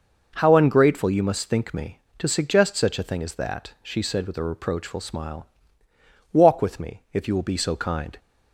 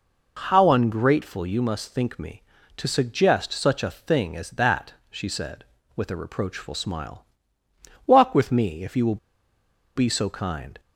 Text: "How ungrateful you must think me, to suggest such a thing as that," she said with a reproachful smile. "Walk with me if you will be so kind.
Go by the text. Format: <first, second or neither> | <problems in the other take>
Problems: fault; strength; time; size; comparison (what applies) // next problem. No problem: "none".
first | pauses between "will" and "be"; noticeable; at 9.1 s; 0.77 s long